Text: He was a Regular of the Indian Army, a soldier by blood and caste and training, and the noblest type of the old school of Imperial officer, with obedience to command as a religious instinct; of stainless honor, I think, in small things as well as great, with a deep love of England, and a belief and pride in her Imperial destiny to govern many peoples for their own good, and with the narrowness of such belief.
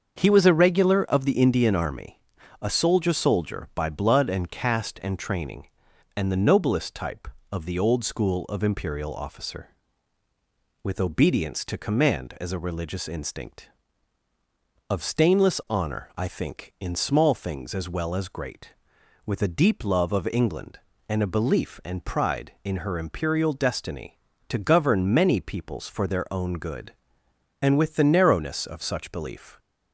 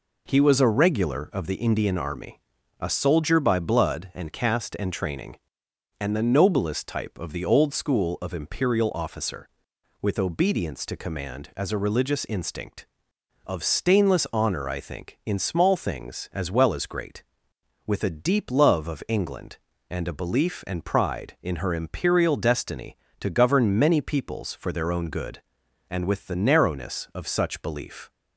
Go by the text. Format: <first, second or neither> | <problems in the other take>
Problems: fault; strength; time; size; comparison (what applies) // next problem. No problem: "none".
second | starts louder than the rest; until 1.1 s; 7 dB // says "soldier" twice; at 3.1 s